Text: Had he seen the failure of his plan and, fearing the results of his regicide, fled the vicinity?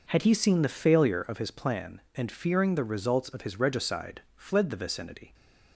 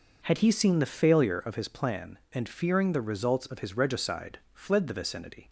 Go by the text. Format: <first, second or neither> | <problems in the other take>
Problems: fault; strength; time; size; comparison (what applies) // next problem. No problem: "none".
neither | none